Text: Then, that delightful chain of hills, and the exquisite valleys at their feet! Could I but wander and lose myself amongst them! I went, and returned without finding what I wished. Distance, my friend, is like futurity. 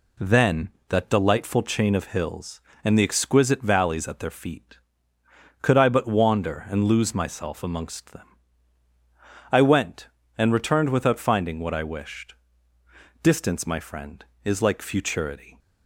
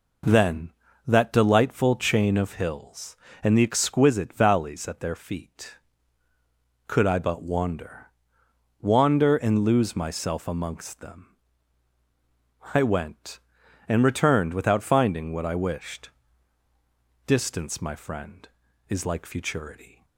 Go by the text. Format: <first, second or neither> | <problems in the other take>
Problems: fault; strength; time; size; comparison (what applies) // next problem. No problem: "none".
first | says "wander" twice; at 8.8 s